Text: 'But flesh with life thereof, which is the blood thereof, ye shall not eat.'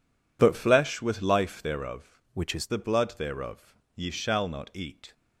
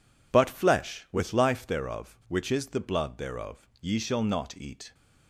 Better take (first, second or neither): second